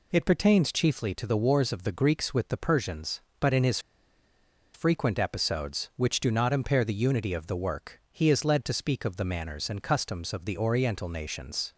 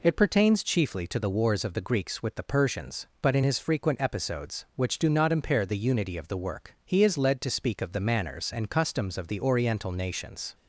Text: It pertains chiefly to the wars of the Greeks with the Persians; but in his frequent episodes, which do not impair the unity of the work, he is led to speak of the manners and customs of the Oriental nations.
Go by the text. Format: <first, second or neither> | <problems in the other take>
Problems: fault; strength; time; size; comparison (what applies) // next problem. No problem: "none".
second | pauses between "his" and "frequent"; noticeable; at 3.7 s; 0.95 s long